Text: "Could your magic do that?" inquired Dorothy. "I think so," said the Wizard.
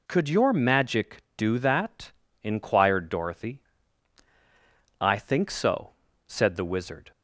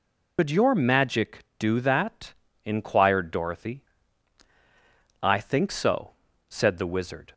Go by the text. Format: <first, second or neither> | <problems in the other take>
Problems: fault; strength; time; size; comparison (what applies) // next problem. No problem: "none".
first | loses the start of "Could"; at 0.3 s; 105 ms